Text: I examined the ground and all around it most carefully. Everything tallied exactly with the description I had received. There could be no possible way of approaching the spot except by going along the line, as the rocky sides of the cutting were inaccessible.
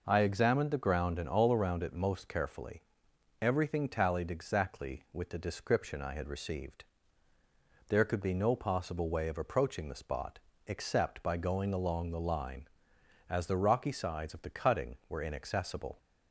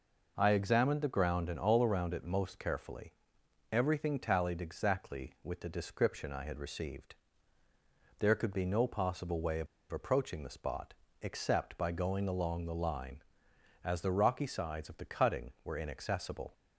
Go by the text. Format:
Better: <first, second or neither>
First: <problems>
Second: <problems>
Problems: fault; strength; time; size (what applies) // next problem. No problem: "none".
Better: first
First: pauses between "spot" and "except"; slight; at 10.3 s; 0.28 s long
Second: pauses between "of" and "approaching"; slight; at 9.6 s; 0.24 s long // pauses between "spot" and "except"; slight; at 10.9 s; 0.28 s long